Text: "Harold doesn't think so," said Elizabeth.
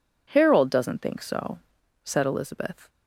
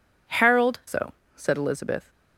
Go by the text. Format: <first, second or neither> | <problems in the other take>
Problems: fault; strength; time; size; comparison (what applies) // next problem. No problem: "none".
first | skips "doesn't think"; at 0.8 s